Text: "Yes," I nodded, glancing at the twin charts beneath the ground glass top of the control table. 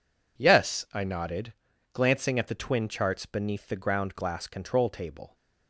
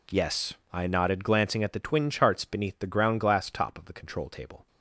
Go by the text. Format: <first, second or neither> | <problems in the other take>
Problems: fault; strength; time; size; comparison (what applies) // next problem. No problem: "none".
second | skips "top of the"; at 4.4 s